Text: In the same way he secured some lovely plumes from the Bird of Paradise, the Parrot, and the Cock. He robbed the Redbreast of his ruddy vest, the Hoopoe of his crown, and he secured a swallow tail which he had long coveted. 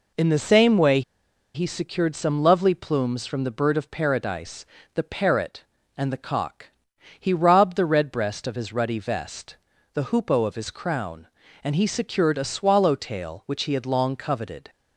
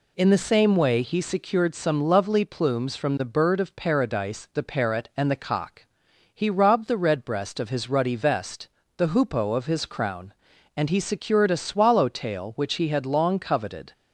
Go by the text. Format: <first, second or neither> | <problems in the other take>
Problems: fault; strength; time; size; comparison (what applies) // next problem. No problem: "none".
second | pauses between "way" and "he"; noticeable; at 1.0 s; 0.53 s long